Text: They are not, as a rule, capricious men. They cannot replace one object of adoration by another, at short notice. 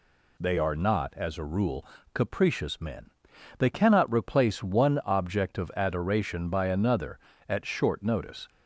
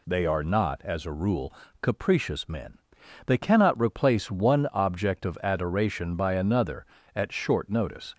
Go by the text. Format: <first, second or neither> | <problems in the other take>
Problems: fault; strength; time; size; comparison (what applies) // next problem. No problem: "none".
neither | none